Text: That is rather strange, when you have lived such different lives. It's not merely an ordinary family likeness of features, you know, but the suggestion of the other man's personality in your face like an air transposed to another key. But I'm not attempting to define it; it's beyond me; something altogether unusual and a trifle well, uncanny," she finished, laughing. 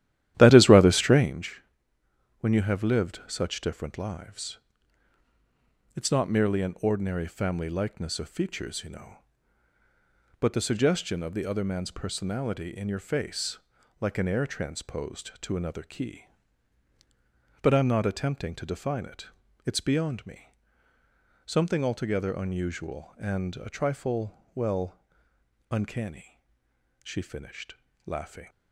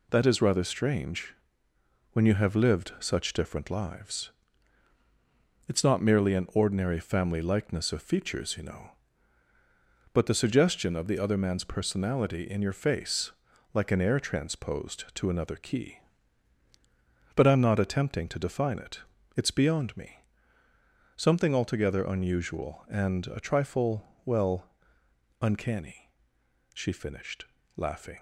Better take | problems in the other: second | starts louder than the rest; strong; until 1.3 s; 13 dB // pauses between "face" and "like"; at 13.5 s; 0.42 s long; also in the second // pauses between "trifle" and "well"; slight; at 24.3 s; 0.20 s long; slight in the second

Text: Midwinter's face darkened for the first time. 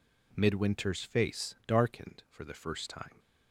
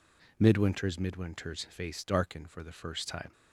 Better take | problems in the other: first | says "Midwinter's" twice; at 0.9 s

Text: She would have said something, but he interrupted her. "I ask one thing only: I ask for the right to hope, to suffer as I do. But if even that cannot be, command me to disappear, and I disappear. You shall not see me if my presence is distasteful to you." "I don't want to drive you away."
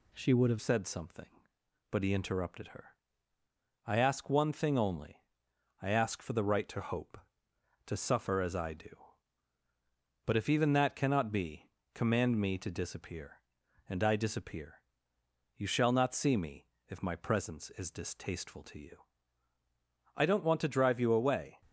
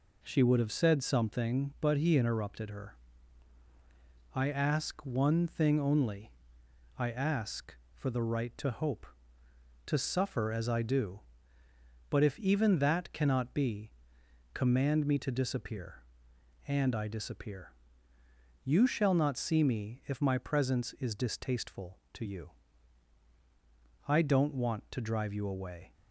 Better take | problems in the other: second | changes voice at "said"; from 0.6 s on; 21.0 s long // pauses between "me" and "if"; slight; at 16.6 s; 0.22 s long

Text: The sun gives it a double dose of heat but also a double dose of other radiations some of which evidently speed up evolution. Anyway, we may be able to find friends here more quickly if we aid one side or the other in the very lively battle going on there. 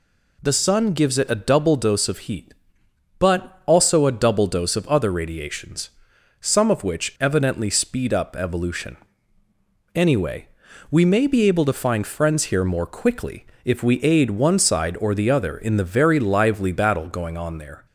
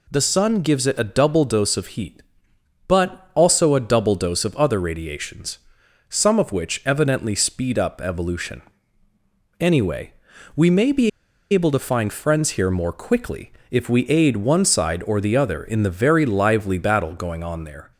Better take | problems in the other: first | pauses between "radiations" and "some"; noticeable; at 5.5 s; 0.50 s long; noticeable in the first // pauses between "be" and "able"; at 11.0 s; 0.43 s long // pauses between "quickly" and "if"; slight; at 13.5 s; 0.18 s long; slight in the first

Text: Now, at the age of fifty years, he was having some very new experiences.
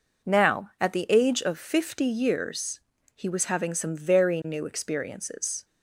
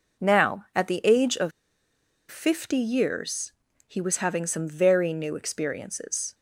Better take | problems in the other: first | pauses between "of" and "fifty"; noticeable; at 1.5 s; 0.79 s long

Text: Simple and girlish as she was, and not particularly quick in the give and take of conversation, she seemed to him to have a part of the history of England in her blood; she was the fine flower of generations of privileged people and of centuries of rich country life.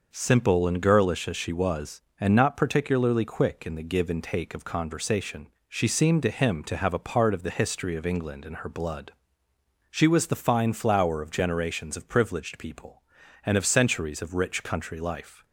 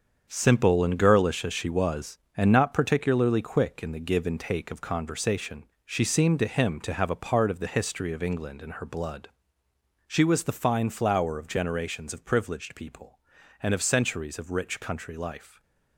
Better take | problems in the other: first | gets quieter; strong; throughout; 9.5 dB

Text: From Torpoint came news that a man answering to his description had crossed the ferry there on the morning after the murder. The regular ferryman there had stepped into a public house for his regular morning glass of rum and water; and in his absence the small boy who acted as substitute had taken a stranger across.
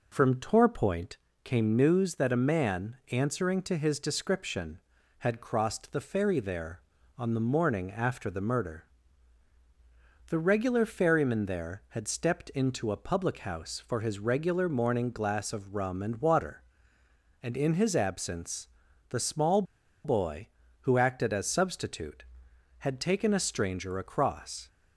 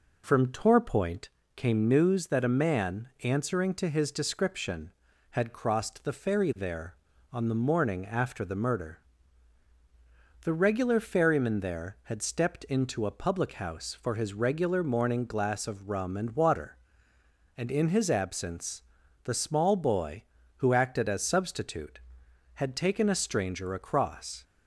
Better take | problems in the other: second | pauses between "Torpoint" and "came"; slight; at 1.1 s; 0.26 s long; slight in the second // pauses between "absence" and "the"; at 18.6 s; 0.42 s long; also in the second // pauses between "small" and "boy"; at 19.6 s; 0.41 s long

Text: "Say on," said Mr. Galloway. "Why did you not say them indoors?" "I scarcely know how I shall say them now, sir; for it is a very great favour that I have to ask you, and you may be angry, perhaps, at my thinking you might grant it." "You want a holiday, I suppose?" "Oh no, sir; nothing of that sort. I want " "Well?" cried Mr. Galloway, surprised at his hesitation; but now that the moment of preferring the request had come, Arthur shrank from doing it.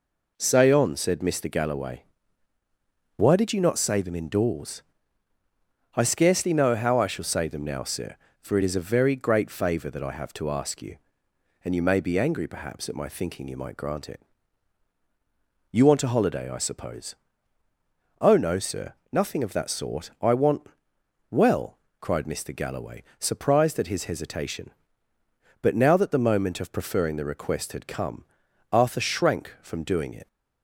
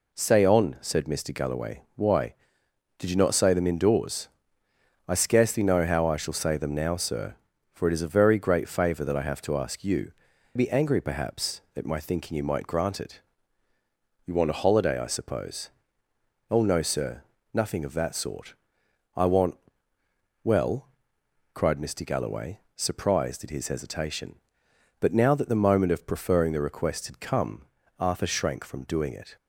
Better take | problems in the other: first | skips "and you may"; at 10.3 s

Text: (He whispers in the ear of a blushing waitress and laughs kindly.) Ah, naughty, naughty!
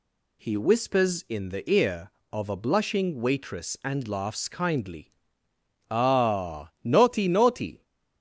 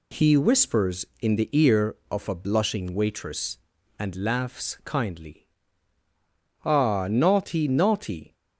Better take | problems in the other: neither | none

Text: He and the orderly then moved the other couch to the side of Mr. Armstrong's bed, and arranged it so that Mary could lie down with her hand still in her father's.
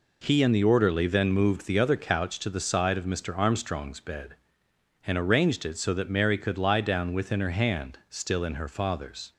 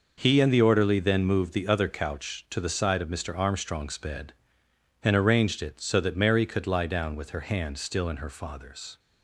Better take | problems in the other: second | says "within" for "with"; at 7.1 s

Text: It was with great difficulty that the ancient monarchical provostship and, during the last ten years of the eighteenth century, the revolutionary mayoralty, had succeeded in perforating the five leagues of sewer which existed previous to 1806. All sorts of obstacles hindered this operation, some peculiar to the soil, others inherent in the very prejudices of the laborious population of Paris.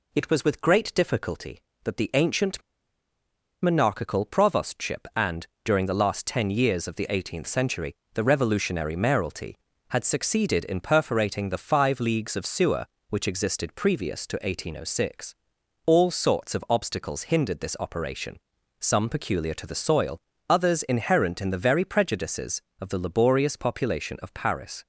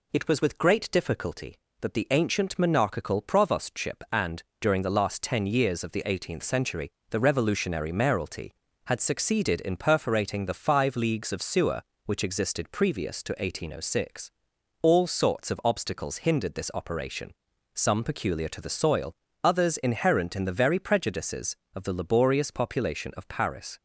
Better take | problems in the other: second | pauses between "ancient" and "monarchical"; at 2.6 s; 1.0 s long

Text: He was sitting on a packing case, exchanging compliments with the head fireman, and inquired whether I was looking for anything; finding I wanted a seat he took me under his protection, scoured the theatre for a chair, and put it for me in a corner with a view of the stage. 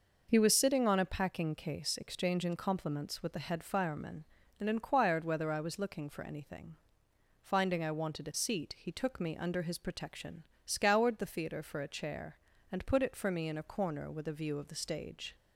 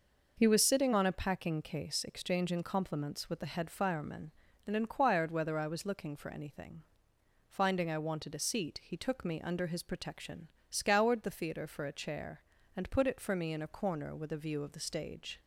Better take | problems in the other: neither | none

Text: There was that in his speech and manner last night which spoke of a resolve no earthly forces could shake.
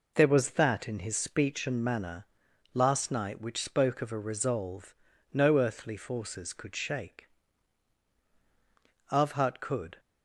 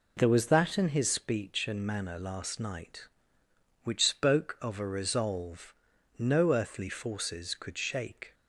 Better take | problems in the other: second | pauses between "manner" and "last"; noticeable; at 2.2 s; 0.46 s long // pauses between "resolve" and "no"; at 4.9 s; 0.38 s long; also in the second // goes on to say "AVhat could"; noticeable; from 9.0 s on; 0.90 s long

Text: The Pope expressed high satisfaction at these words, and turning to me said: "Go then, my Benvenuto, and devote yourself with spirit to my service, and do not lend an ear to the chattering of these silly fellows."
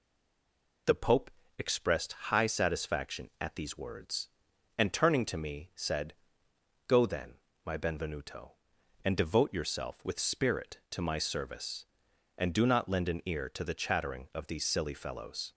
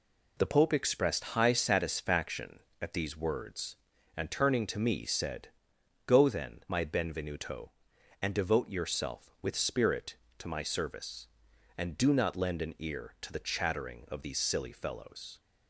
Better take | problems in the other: second | stays silent before the first word; slight; until 0.8 s; 0.8 s long // pauses between "Pope" and "expressed"; slight; at 1.2 s; 0.30 s long

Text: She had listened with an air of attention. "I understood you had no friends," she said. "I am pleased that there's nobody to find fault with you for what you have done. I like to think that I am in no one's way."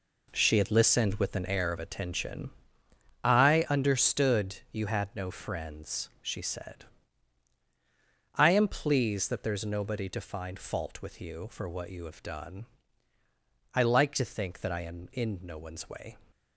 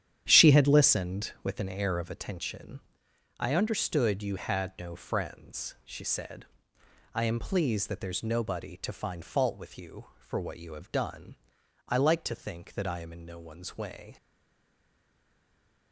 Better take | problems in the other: first | starts louder than the rest; strong; until 1.2 s; 10 dB // stays silent after the last word; noticeable; from 14.1 s on; 1.8 s long

